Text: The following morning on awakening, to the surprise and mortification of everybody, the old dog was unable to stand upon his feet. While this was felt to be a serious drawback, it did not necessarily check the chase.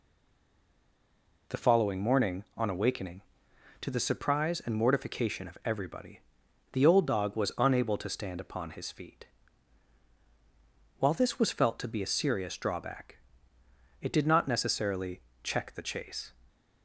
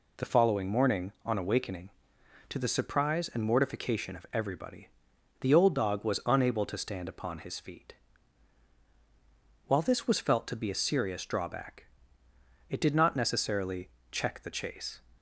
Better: second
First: stays silent before the first word; noticeable; until 1.4 s; 1.4 s long // pauses between "necessarily" and "check"; slight; at 15.1 s; 0.24 s long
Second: pauses between "necessarily" and "check"; slight; at 13.8 s; 0.24 s long

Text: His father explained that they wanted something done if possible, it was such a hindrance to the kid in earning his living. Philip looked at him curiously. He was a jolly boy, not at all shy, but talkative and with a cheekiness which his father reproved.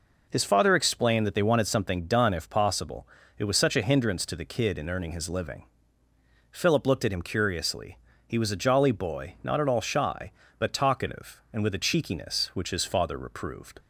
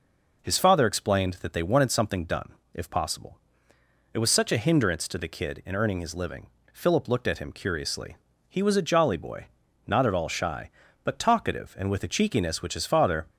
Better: first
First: none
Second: pauses between "done" and "if"; slight; at 2.5 s; 0.22 s long // stops before "reproved"; at 13.2 s

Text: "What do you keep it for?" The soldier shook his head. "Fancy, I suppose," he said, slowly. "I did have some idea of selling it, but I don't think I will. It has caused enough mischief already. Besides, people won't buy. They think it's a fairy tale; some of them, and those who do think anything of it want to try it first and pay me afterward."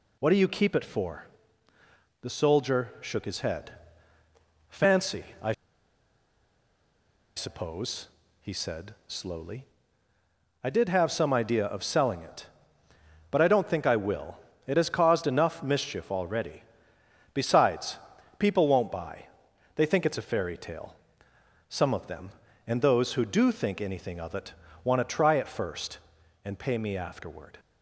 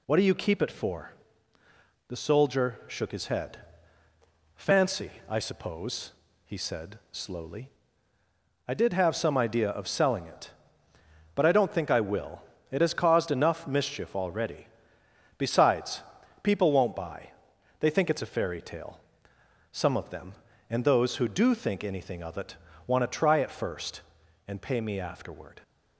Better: second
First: pauses between "I" and "suppose"; strong; at 5.5 s; 1.8 s long // pauses between "it" and "want"; slight; at 24.5 s; 0.30 s long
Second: pauses between "it" and "want"; slight; at 22.5 s; 0.30 s long

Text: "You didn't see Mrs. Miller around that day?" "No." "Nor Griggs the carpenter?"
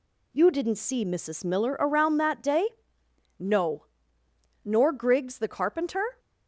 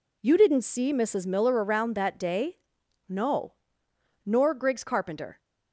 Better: first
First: none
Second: skips "the"; at 4.8 s

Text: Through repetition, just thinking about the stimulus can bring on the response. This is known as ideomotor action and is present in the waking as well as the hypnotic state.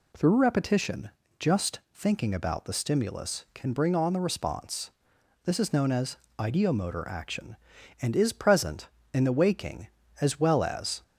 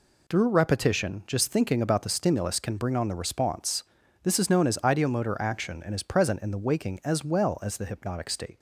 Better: second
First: pauses between "as" and "ideomotor"; slight; at 6.1 s; 0.22 s long // stops before "the hypnotic state"; at 11.0 s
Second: none

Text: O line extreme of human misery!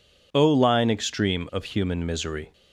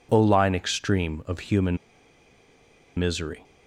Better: first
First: none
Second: pauses between "human" and "misery"; at 1.7 s; 1.1 s long

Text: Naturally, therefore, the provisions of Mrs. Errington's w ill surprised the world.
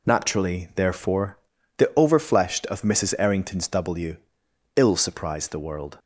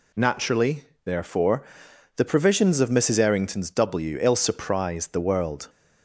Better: second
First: says "overfleshed" for "provisions"; at 1.9 s // pauses between "w" and "ill"; noticeable; at 4.1 s; 0.58 s long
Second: none

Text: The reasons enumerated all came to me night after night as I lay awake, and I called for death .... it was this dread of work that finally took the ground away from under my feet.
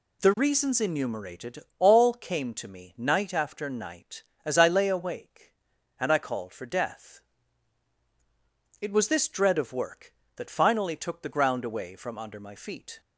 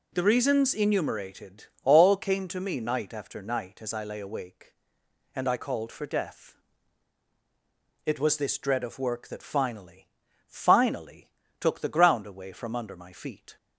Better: first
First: pauses between "enumerated" and "all"; slight; at 1.6 s; 0.18 s long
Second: pauses between "enumerated" and "all"; slight; at 1.6 s; 0.18 s long // says "finally" twice; at 10.4 s

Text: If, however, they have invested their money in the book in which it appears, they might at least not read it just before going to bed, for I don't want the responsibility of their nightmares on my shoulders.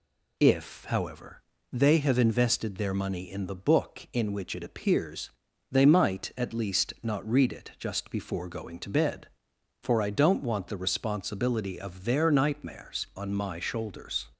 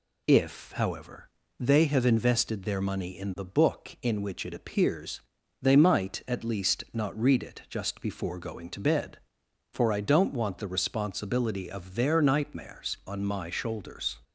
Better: neither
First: none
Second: none

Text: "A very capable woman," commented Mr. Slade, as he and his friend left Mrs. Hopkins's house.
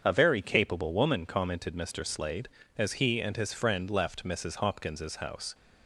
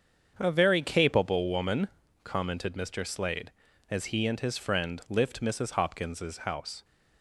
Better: first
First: starts louder than the rest; strong; until 1.0 s; 7 dB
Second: starts louder than the rest; until 1.3 s; 7 dB // says "lift" for "left"; at 5.0 s

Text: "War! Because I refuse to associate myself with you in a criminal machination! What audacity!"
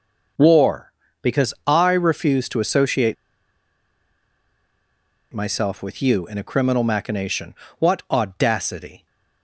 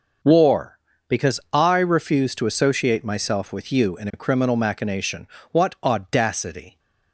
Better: second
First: pauses between "associate" and "myself"; strong; at 3.1 s; 2.1 s long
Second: none

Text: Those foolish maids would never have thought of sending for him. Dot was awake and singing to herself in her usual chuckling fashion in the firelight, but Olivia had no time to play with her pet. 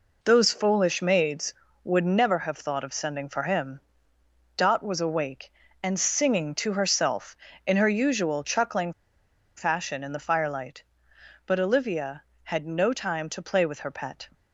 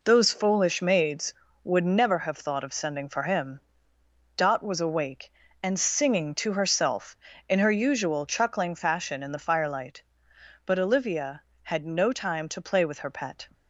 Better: second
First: pauses between "chuckling" and "fashion"; noticeable; at 8.9 s; 0.63 s long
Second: none

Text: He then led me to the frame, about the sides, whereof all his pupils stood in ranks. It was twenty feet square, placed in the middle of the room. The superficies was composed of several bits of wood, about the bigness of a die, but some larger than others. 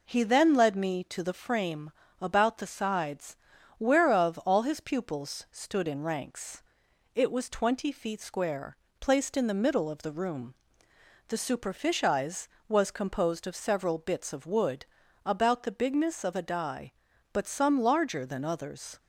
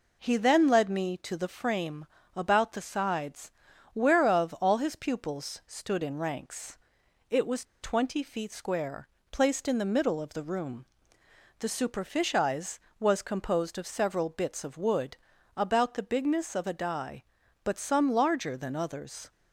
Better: first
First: none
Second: pauses between "was" and "twenty"; slight; at 7.6 s; 0.18 s long

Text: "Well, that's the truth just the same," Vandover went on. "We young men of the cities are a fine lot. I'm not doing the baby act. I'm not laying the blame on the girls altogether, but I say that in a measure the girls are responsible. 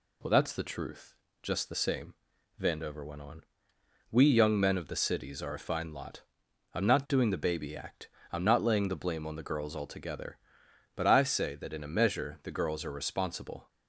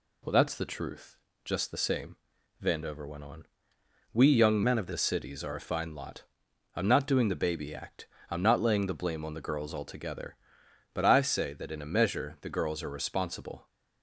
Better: first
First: pauses between "truth" and "just"; slight; at 1.1 s; 0.26 s long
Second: pauses between "truth" and "just"; slight; at 1.1 s; 0.26 s long // changes voice from "men" to "the"; from 4.6 to 4.9 s; 0.3 s long

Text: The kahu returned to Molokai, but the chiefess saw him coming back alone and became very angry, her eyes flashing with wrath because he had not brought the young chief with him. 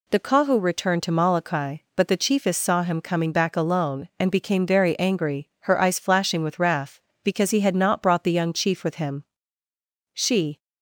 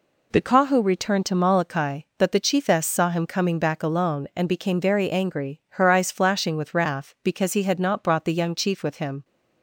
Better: second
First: goes on to say "She"; slight; from 10.1 s on; 0.46 s long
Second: none

